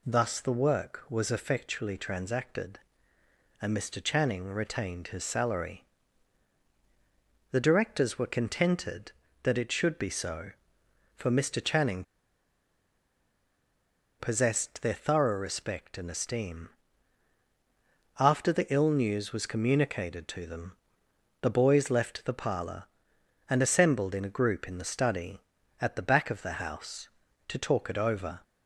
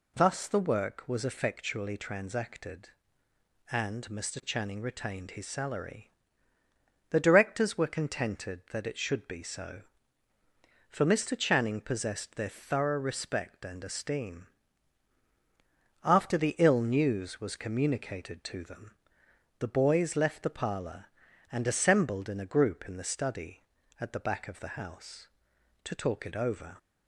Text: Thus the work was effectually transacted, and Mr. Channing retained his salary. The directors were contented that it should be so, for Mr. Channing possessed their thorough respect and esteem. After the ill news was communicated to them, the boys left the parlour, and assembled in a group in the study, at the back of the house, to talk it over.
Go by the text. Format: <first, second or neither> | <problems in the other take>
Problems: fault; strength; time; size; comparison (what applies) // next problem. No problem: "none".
second | pauses between "Channing" and "possessed"; strong; at 12.0 s; 2.1 s long